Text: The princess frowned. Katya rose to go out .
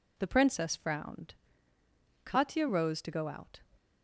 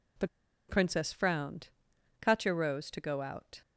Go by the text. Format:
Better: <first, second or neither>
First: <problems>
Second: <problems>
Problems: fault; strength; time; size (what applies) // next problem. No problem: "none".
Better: first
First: none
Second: pauses between "The" and "princess"; at 0.2 s; 0.41 s long